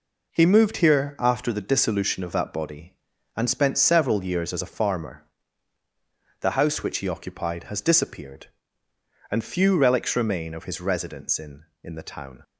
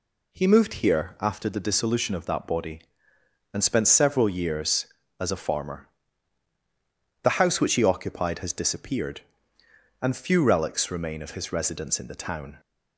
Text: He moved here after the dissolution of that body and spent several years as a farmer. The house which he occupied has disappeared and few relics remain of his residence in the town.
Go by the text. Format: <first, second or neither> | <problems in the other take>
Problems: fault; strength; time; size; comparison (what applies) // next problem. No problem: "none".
second | says "in" twice; at 11.8 s